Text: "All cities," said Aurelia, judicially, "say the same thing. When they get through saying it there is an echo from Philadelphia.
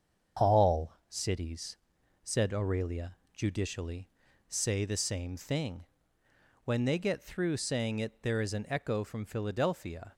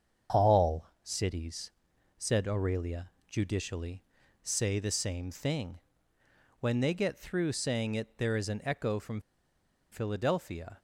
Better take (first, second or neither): first